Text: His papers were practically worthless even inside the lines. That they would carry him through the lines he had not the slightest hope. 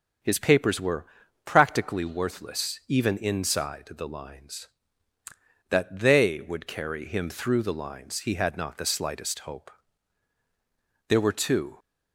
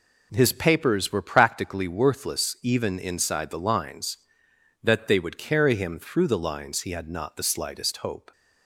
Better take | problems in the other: second | starts louder than the rest; strong; until 1.6 s; 7.5 dB // pauses between "were" and "practically"; at 1.0 s; 0.40 s long // goes on to say "There were two"; noticeable; from 11.0 s on; 0.70 s long

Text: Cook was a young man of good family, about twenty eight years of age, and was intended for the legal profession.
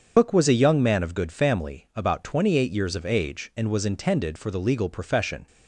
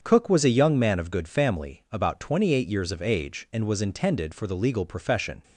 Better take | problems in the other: second | loses the start of "Cook"; at 0.1 s; 100 ms // starts louder than the rest; until 1.1 s; 7 dB; strong in the second

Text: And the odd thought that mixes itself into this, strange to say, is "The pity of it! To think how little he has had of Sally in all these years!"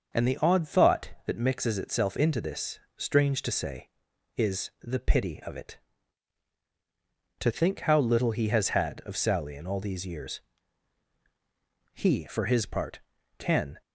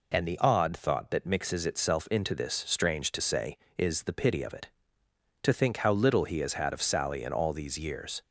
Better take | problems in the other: second | starts louder than the rest; until 1.3 s; 6 dB // goes on to say "He for his part can"; strong; from 11.9 s on; 1.8 s long

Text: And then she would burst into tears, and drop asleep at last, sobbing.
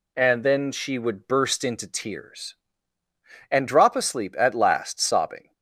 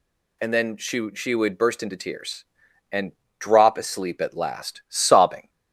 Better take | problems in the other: first | says "she" twice; at 1.1 s // pauses between "and" and "drop"; slight; at 3.1 s; 0.28 s long

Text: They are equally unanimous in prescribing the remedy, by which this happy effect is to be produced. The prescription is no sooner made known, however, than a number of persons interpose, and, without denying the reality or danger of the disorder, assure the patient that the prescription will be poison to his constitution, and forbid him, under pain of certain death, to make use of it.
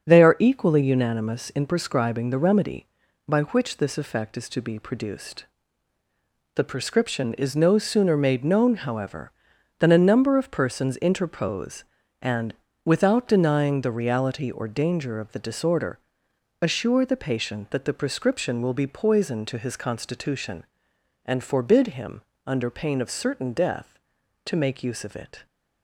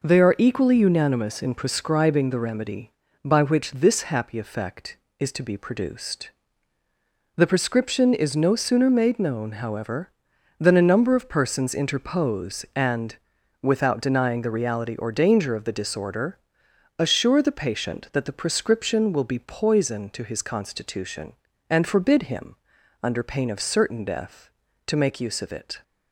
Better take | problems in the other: second | starts louder than the rest; until 1.0 s; 7 dB // skips "happy"; at 3.9 s

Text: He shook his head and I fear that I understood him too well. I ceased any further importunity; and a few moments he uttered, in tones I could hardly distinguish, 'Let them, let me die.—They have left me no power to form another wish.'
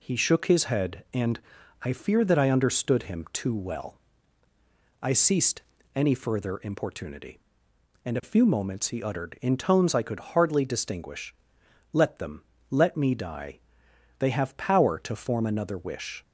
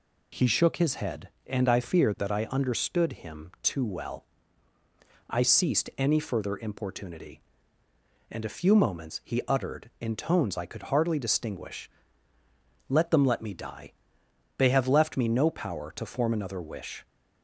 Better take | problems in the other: second | pauses between "and" and "I"; at 1.3 s; 0.44 s long // pauses between "ceased" and "any"; slight; at 5.6 s; 0.34 s long // skips "left me no"; at 14.5 s

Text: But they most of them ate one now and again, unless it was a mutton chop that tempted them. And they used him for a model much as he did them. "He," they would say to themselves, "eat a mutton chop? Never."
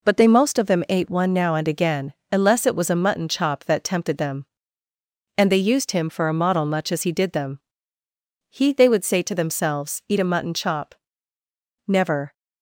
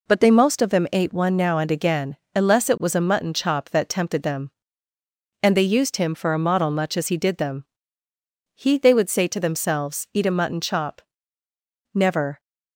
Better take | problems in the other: neither | none

